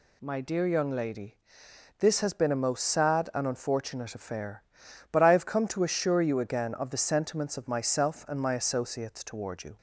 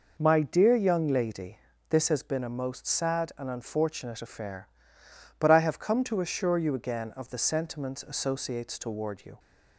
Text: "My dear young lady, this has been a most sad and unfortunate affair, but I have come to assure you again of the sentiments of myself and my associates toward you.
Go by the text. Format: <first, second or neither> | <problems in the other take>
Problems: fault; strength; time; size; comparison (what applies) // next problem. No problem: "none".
first | skips "of myself and my"; at 8.0 s